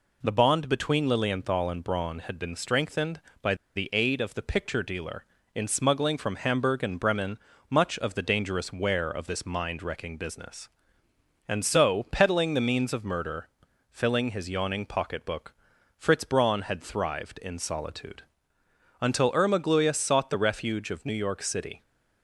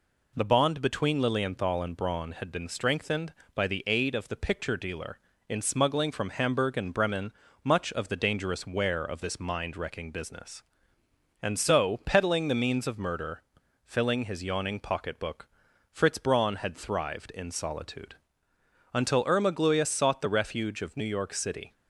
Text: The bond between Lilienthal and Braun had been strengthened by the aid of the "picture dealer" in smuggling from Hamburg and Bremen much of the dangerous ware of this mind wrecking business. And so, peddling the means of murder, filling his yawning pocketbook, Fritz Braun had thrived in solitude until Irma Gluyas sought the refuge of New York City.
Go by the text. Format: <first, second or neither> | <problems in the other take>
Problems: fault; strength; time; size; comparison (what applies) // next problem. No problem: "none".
second | pauses between "by" and "the"; slight; at 3.5 s; 0.20 s long // pauses between "Bremen" and "much"; slight; at 7.3 s; 0.30 s long; slight in the second // pauses between "solitude" and "until"; noticeable; at 18.2 s; 0.80 s long; noticeable in the second